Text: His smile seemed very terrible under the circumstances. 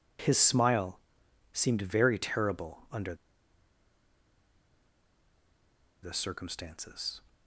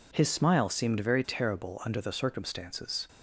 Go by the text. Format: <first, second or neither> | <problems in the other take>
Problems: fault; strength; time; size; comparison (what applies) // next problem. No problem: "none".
second | pauses between "smile" and "seemed"; noticeable; at 1.0 s; 0.54 s long // pauses between "under" and "the"; strong; at 3.1 s; 2.8 s long